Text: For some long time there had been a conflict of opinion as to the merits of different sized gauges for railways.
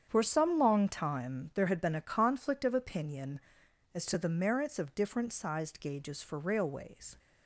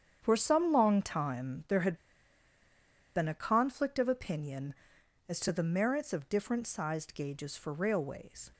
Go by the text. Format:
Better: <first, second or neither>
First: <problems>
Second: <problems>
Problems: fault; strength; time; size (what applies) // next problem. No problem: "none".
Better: first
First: starts louder than the rest; strong; until 1.0 s; 8.5 dB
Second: starts louder than the rest; strong; until 1.2 s; 8.5 dB // pauses between "had" and "been"; at 1.9 s; 1.1 s long